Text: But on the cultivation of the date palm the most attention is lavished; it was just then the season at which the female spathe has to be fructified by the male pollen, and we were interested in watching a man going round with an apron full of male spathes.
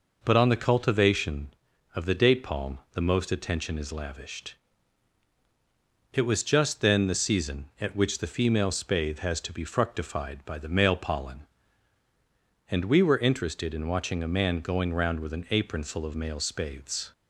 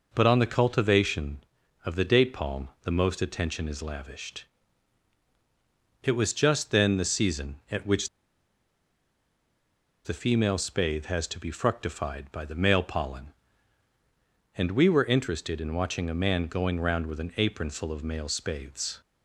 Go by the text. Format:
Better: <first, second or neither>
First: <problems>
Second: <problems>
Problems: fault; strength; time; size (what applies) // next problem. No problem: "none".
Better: first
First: none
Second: pauses between "which" and "the"; strong; at 8.0 s; 1.9 s long